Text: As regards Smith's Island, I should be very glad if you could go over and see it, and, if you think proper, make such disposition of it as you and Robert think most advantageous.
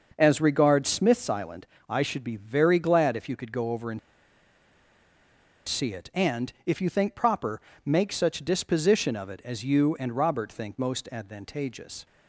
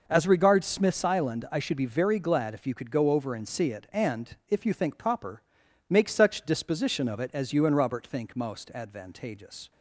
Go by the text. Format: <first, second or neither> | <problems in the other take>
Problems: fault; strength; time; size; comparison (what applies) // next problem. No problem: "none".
second | starts louder than the rest; until 1.1 s; 6 dB // pauses between "and" and "see"; strong; at 3.9 s; 1.6 s long